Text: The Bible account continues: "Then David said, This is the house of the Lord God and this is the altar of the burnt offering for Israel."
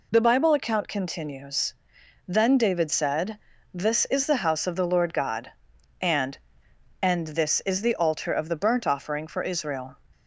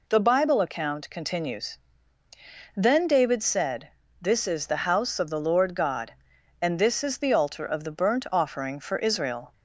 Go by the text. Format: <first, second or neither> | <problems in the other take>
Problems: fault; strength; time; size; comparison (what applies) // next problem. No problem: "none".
second | says "and" twice; at 6.9 s